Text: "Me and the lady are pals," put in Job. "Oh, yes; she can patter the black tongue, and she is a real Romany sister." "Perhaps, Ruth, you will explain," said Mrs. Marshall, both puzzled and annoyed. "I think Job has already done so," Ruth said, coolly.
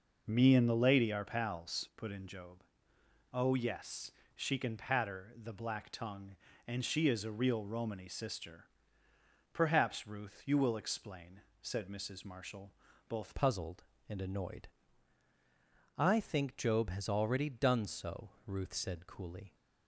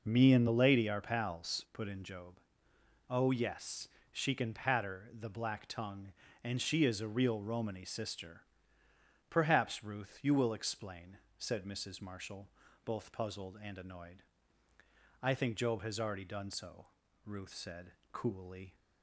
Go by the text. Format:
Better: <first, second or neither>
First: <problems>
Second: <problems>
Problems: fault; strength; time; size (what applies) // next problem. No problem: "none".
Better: second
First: changes voice at "puzzled"; from 13.3 s on; 6.2 s long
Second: none